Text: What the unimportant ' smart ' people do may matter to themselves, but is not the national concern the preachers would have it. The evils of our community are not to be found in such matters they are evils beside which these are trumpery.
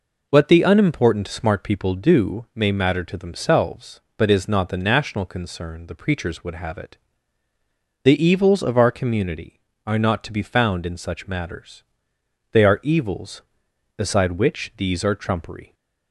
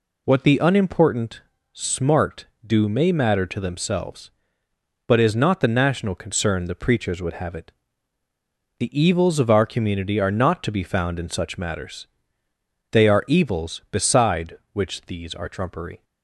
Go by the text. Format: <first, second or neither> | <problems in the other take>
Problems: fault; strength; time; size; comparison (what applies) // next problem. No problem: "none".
first | skips "people"; at 2.6 s // pauses between "matters" and "they"; noticeable; at 12.0 s; 0.84 s long; noticeable in the first